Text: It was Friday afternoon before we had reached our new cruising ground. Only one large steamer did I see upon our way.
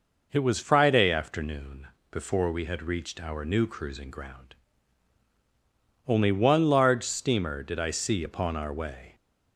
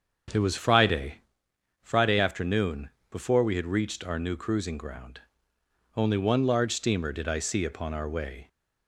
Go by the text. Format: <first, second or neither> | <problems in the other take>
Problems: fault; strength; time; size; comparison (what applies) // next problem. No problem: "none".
first | starts louder than the rest; until 1.9 s; 7 dB // says "Friday" twice; at 1.8 s // pauses between "afternoon" and "before"; slight; at 2.8 s; 0.22 s long; slight in the first